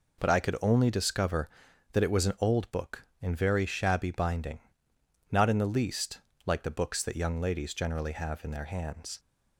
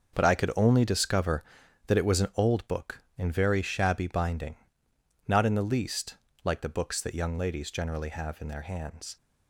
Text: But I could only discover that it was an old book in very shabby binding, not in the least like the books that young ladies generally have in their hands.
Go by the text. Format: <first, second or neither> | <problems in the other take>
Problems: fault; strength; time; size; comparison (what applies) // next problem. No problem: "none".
first | gets quieter; strong; throughout; 10.5 dB // pauses between "least" and "like"; slight; at 6.1 s; 0.28 s long; slight in the first